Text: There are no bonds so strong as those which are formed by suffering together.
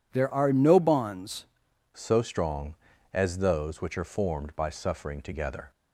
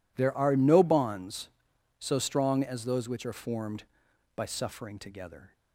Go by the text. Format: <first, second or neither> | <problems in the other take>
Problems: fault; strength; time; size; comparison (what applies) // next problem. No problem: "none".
second | changes voice at "so"; from 1.9 s on; 3.8 s long